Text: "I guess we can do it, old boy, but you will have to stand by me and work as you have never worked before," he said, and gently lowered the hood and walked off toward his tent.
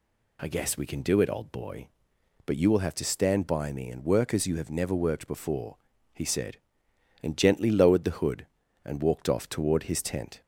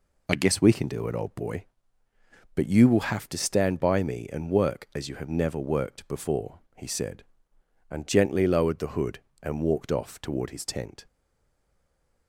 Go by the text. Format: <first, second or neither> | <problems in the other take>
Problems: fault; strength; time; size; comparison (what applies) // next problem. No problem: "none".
first | stays silent after the last word; noticeable; from 11.0 s on; 1.2 s long